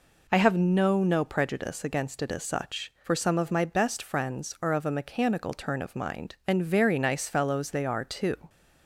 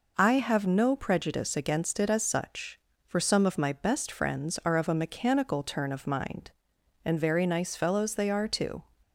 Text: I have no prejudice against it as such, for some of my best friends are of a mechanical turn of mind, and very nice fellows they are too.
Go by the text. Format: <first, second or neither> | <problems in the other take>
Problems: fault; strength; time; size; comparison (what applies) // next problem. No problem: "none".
second | says "no" twice; at 1.0 s